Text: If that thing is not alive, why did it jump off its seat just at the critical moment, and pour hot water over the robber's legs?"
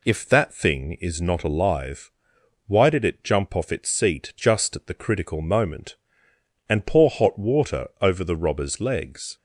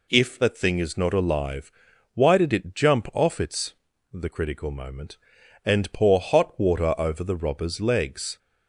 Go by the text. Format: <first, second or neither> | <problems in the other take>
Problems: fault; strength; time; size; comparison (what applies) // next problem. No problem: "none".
first | skips "seat just at"; at 3.9 s